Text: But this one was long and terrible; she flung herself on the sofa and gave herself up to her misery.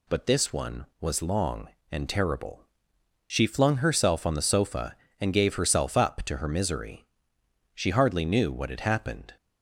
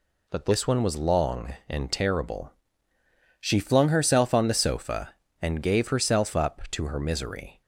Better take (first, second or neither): second